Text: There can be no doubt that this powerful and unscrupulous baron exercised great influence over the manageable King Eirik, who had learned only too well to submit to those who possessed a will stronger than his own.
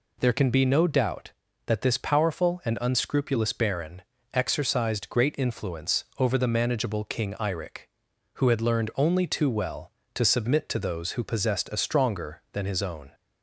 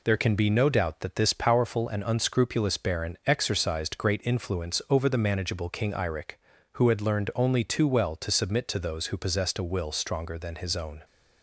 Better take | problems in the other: second | pauses between "baron" and "exercised"; slight; at 4.0 s; 0.32 s long // skips "will"; at 11.7 s

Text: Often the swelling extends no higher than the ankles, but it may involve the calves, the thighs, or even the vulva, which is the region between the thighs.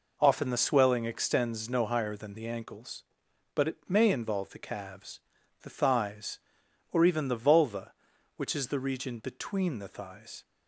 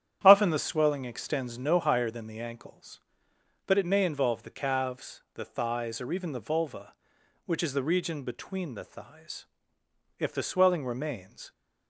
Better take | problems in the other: first | starts louder than the rest; strong; until 1.2 s; 10 dB // goes on to say "If the swelling remains"; from 10.1 s on; 1.3 s long

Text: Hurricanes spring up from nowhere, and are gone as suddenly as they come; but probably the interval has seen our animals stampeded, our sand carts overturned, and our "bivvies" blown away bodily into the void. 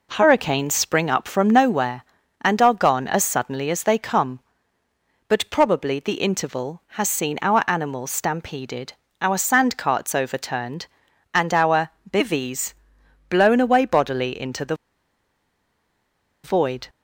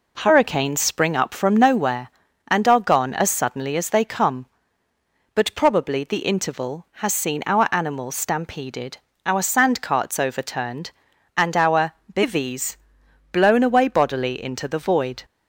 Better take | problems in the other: second | pauses between "our" and "bivvies"; slight; at 11.8 s; 0.20 s long; slight in the second // pauses between "bivvies" and "blown"; noticeable; at 12.7 s; 0.56 s long; noticeable in the second // pauses between "the" and "void"; strong; at 14.7 s; 1.6 s long

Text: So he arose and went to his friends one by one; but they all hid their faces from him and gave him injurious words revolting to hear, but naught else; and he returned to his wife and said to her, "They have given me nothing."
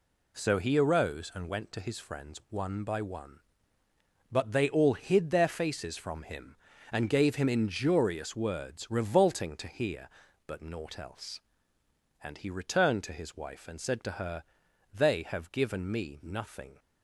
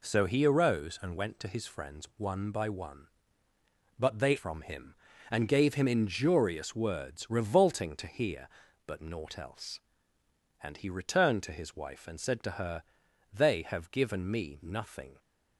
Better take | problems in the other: first | skips "all hid their faces"; at 4.3 s

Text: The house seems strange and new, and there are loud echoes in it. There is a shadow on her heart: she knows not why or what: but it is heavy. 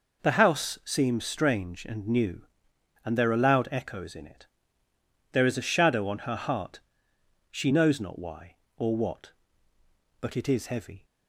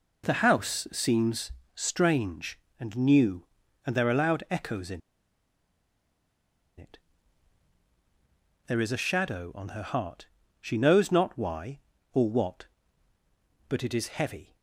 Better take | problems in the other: first | pauses between "seems" and "strange"; slight; at 1.5 s; 0.24 s long // pauses between "in" and "it"; strong; at 5.0 s; 1.7 s long

